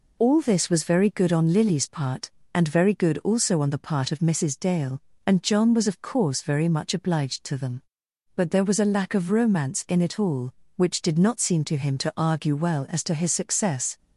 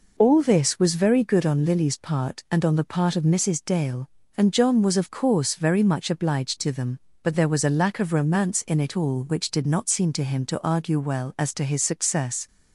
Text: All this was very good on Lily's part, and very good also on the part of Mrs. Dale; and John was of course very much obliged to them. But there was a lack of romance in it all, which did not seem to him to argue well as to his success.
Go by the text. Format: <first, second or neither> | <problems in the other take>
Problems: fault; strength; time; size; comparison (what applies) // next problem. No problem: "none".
first | skips "very good also"; at 2.6 s